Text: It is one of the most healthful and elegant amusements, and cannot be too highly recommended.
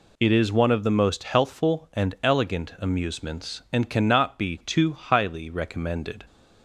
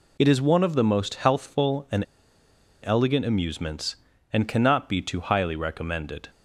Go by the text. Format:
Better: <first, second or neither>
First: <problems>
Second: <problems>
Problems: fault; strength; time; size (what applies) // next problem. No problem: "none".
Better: first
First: none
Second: pauses between "and" and "elegant"; noticeable; at 2.0 s; 0.81 s long